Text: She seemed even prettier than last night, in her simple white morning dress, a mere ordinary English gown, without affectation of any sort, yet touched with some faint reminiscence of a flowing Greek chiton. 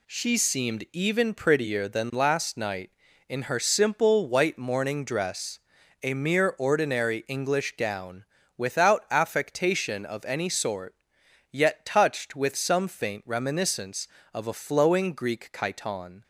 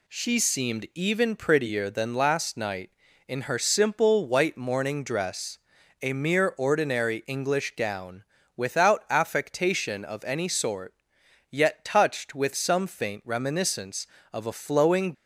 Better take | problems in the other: first | stops before "Greek chiton"; at 15.1 s

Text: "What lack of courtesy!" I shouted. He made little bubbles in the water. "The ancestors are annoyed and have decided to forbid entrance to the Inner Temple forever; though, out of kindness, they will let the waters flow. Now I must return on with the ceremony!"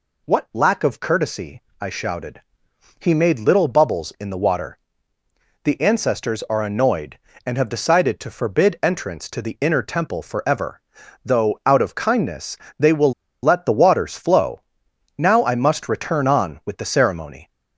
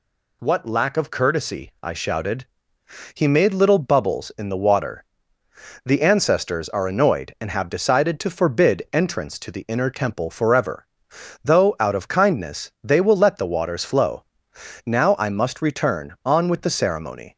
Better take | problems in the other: second | pauses between "will" and "let"; slight; at 13.1 s; 0.29 s long

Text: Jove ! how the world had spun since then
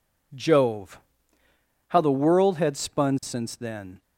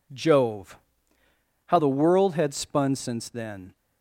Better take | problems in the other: neither | none

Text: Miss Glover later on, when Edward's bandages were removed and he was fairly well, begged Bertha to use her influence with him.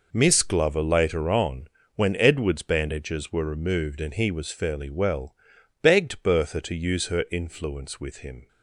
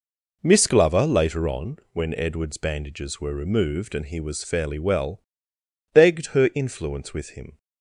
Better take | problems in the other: first | skips "Bertha to use"; at 6.2 s

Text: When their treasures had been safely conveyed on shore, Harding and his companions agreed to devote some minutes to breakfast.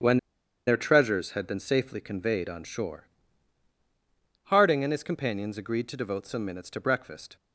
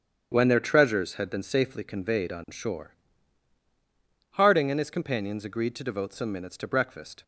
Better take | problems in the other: second | starts louder than the rest; strong; until 1.5 s; 9 dB; strong in the second // pauses between "When" and "their"; noticeable; at 0.1 s; 0.49 s long

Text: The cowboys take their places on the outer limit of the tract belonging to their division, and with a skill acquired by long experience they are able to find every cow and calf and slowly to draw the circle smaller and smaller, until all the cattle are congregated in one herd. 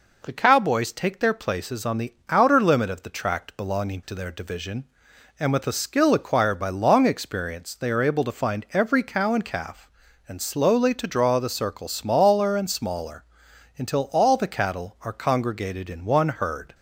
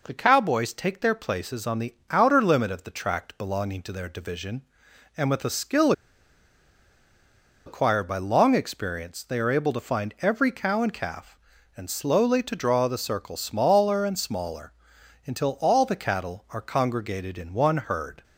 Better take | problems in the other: first | pauses between "the" and "outer"; slight; at 1.9 s; 0.16 s long; slight in the first // pauses between "skill" and "acquired"; strong; at 5.9 s; 1.7 s long

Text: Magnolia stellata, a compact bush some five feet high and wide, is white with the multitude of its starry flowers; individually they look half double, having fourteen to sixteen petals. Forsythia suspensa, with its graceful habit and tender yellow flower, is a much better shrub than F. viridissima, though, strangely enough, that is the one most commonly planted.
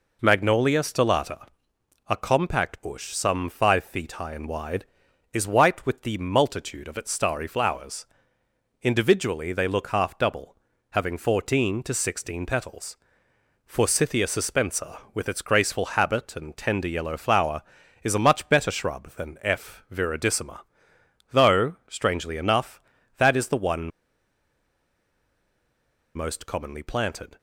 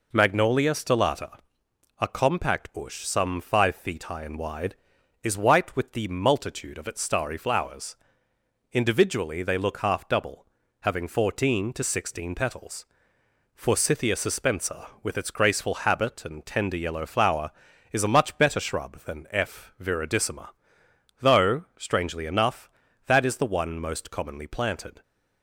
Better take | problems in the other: second | pauses between "one" and "most"; strong; at 23.8 s; 2.2 s long

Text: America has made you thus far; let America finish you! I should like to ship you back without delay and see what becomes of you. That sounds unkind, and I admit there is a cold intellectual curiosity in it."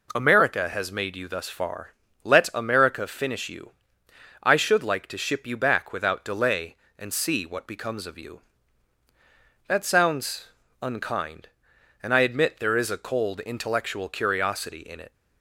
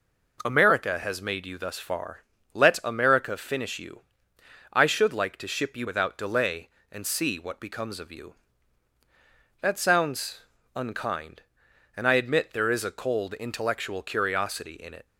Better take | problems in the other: first | skips "back"; at 5.8 s // pauses between "sounds" and "unkind"; slight; at 10.4 s; 0.34 s long; slight in the first

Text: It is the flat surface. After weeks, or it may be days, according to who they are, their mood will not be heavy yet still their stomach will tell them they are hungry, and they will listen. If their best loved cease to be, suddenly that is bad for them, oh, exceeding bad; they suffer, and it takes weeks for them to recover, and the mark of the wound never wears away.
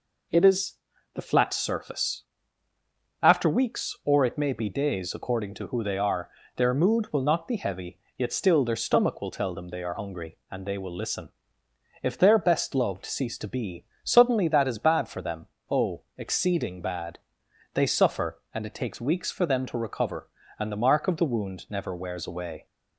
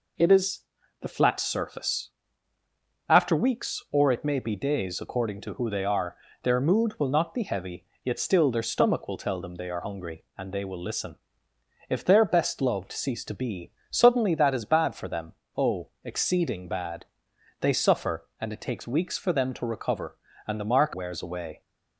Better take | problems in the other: first | pauses between "is" and "the"; at 0.6 s; 0.40 s long; also in the first // pauses between "heavy" and "yet"; slight; at 7.8 s; 0.18 s long; slight in the first // skips "of the wound never"; at 20.9 s

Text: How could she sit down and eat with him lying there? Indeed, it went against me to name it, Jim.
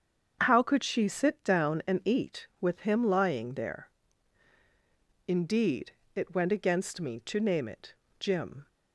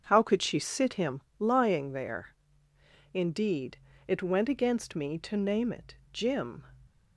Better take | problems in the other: first | starts louder than the rest; until 1.0 s; 6.5 dB; strong in the first // skips "down and eat with"; at 0.9 s // pauses between "him" and "lying"; slight; at 1.2 s; 0.18 s long

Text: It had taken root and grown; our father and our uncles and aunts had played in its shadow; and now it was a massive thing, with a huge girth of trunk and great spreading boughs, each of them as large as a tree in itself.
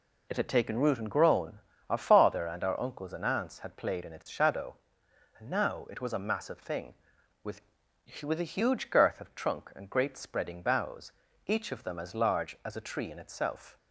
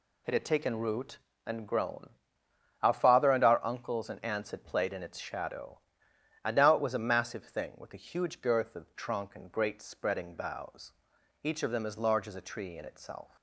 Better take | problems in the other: second | says "with" twice; at 8.2 s

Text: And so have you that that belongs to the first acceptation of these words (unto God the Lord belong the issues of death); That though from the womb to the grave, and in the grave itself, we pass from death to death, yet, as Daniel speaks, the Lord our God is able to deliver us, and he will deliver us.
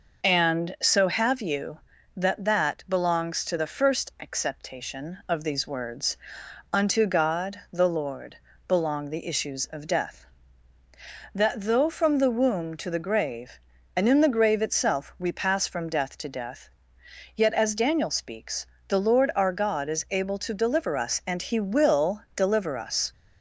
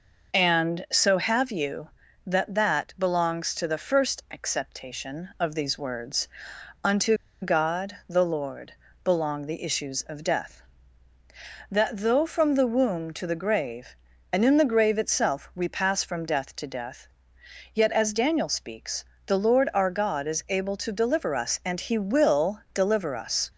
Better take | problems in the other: first | pauses between "unto" and "God"; slight; at 7.1 s; 0.26 s long // pauses between "Lord" and "belong"; slight; at 8.7 s; 0.32 s long; slight in the first

